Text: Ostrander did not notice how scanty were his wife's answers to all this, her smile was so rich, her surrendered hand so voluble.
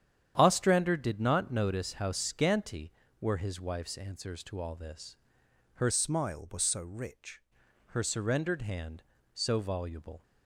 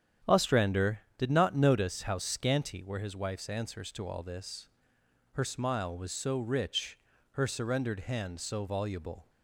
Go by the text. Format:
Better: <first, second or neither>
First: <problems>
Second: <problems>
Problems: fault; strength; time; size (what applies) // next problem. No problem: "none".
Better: second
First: starts louder than the rest; strong; until 1.3 s; 9.5 dB // changes voice from "smile" to "rich"; from 5.9 to 7.4 s; 1.5 s long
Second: starts louder than the rest; strong; until 1.4 s; 9.5 dB